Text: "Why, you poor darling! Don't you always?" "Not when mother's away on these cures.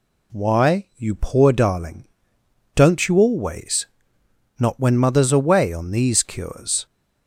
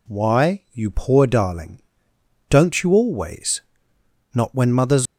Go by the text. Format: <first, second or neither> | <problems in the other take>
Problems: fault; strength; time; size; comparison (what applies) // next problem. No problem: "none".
first | stops before "away on these cures"; at 5.0 s